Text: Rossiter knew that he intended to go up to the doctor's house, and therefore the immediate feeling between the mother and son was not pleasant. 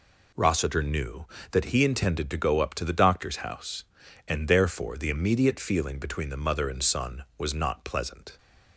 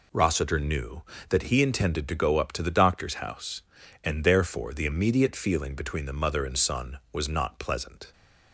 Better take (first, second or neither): neither